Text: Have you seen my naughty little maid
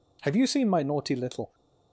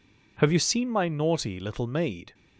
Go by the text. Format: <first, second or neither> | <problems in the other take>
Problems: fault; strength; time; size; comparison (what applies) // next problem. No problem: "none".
second | stops before "maid"; at 1.5 s